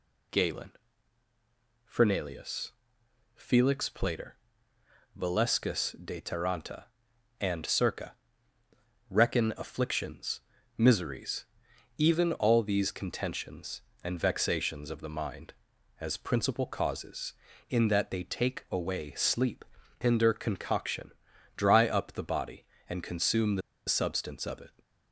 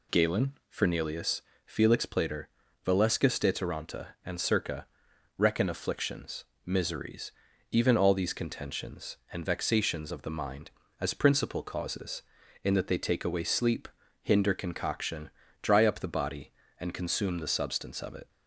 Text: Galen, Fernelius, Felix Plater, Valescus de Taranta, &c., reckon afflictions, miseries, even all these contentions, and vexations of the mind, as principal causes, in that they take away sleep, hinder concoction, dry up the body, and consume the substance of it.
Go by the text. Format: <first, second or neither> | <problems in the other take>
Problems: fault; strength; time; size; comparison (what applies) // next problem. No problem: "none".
second | pauses between "the" and "substance"; slight; at 23.6 s; 0.27 s long